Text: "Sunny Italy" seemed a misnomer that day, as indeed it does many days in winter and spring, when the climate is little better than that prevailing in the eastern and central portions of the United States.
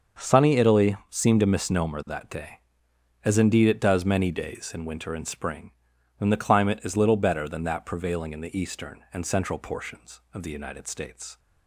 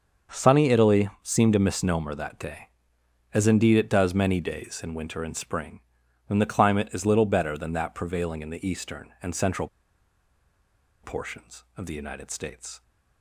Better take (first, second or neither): first